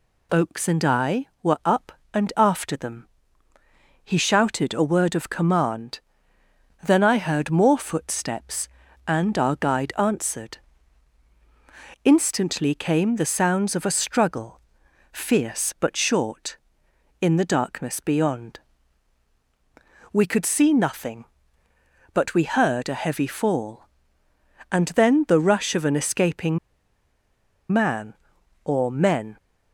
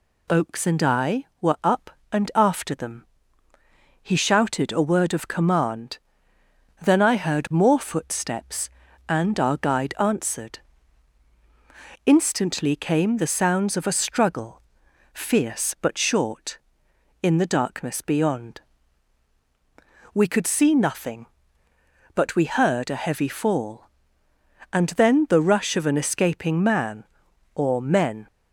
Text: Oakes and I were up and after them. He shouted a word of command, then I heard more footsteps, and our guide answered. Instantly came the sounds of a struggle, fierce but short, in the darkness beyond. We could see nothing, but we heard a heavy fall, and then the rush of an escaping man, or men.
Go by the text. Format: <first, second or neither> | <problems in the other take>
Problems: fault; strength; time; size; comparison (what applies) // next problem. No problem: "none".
second | pauses between "escaping" and "man"; at 26.5 s; 1.1 s long